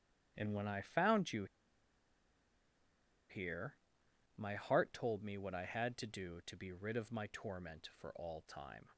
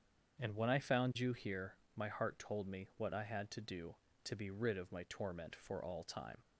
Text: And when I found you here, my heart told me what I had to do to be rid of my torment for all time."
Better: second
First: starts louder than the rest; strong; until 1.3 s; 10.5 dB // pauses between "you" and "here"; strong; at 1.4 s; 1.8 s long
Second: starts louder than the rest; strong; until 1.4 s; 7.5 dB

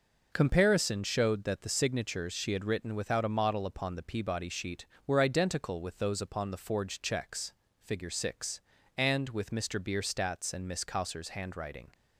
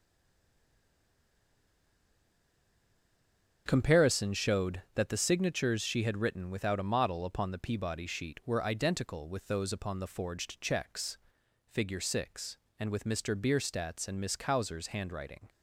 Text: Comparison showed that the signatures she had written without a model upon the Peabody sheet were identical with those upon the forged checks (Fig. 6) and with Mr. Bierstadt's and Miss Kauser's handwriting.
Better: first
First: none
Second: stays silent before the first word; strong; until 3.6 s; 3.6 s long // starts louder than the rest; until 4.6 s; 7 dB

